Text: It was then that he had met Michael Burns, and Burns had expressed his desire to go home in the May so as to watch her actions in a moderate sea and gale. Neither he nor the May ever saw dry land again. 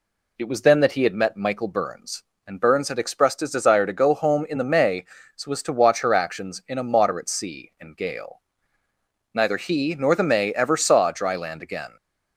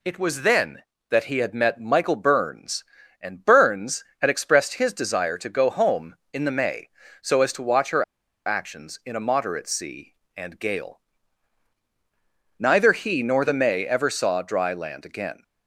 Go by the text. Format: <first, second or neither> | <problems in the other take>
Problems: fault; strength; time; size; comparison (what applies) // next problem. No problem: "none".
first | pauses between "her" and "actions"; at 8.0 s; 0.43 s long